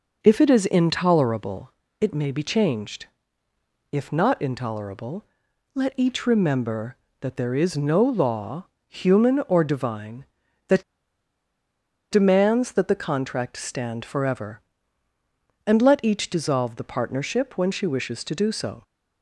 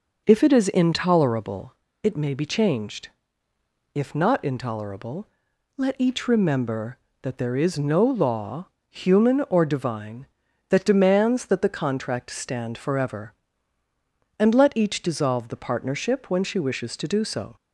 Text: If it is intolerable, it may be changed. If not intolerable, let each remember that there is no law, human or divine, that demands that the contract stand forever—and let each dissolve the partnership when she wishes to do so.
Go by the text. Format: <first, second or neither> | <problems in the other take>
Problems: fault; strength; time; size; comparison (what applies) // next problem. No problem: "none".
second | pauses between "that" and "demands"; strong; at 10.8 s; 1.2 s long